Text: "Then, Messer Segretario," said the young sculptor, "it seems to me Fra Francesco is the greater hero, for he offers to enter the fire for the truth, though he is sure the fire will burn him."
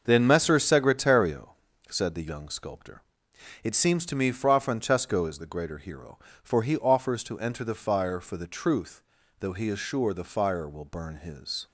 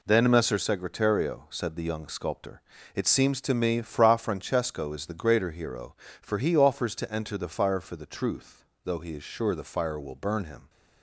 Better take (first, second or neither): second